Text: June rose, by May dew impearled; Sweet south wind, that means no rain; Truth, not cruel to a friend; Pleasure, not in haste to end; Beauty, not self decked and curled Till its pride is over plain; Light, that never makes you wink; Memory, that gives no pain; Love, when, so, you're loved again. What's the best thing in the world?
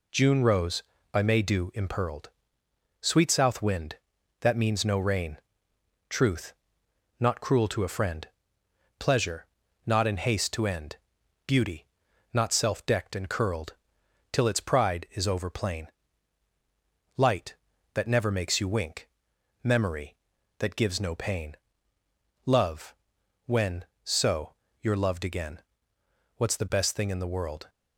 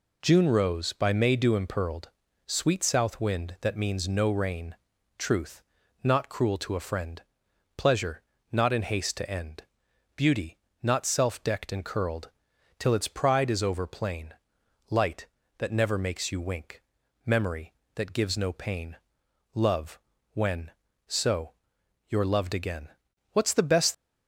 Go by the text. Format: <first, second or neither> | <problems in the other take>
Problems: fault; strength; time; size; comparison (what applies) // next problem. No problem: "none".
first | pauses between "curled" and "Till"; noticeable; at 12.3 s; 0.48 s long; noticeable in the first // stops before "thing in the world"; at 23.9 s